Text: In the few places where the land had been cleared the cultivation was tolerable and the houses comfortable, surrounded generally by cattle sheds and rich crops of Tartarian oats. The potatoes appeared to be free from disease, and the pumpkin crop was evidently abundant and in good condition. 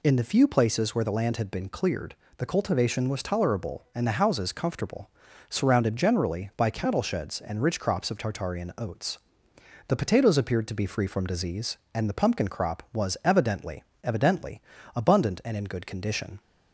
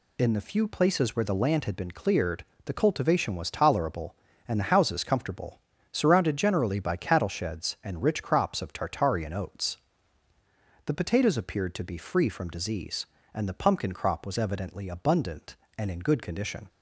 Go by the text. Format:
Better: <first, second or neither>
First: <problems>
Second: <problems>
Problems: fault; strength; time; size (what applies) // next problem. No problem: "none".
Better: second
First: pauses between "cleared" and "the"; slight; at 2.1 s; 0.22 s long // says "evidently" twice; at 14.0 s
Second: pauses between "cleared" and "the"; slight; at 2.4 s; 0.20 s long